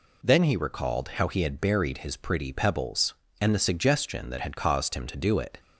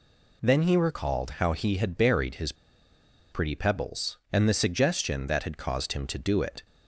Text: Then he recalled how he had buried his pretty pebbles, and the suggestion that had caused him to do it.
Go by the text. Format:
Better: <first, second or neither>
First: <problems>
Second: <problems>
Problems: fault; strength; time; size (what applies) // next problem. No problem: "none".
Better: first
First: none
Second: pauses between "his" and "pretty"; noticeable; at 2.5 s; 0.78 s long